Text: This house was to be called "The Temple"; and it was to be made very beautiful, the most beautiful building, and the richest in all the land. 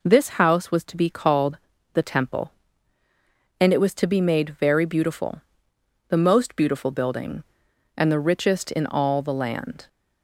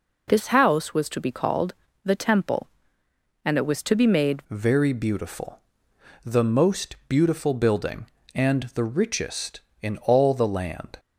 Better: first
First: pauses between "called" and "The"; slight; at 1.5 s; 0.34 s long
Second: pauses between "called" and "The"; slight; at 1.7 s; 0.32 s long // changes voice at "very"; from 4.4 s on; 6.4 s long

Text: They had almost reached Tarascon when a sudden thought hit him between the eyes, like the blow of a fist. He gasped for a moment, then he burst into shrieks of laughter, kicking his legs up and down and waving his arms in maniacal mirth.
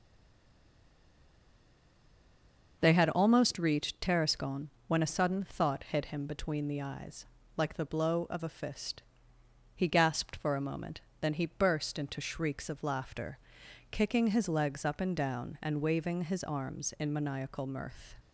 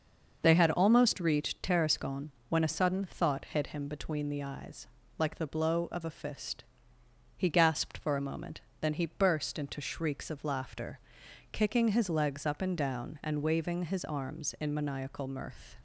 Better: second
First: stays silent before the first word; strong; until 2.7 s; 2.7 s long // starts louder than the rest; noticeable; until 3.8 s; 6 dB // pauses between "Tarascon" and "when"; slight; at 4.6 s; 0.16 s long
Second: starts louder than the rest; noticeable; until 1.4 s; 6 dB // pauses between "Tarascon" and "when"; slight; at 2.3 s; 0.16 s long

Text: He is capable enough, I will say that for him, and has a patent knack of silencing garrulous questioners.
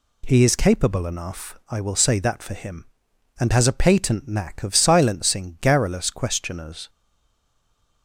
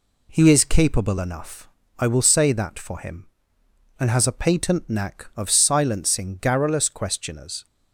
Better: second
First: stays silent after the last word; from 6.8 s on; 1.2 s long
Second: none

